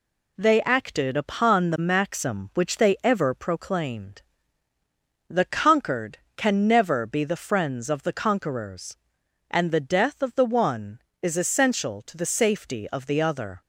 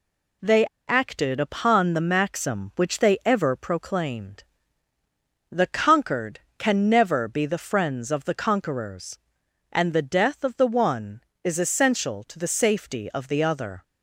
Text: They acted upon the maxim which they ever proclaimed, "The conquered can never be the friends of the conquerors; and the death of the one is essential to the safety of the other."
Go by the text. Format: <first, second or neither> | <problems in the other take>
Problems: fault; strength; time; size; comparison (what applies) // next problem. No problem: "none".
first | pauses between "They" and "acted"; slight; at 0.6 s; 0.21 s long